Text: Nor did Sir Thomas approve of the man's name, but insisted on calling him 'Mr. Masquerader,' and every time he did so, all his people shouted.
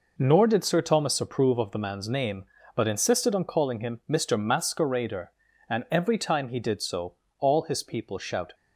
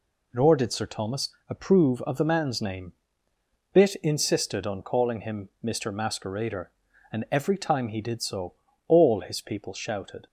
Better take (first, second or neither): first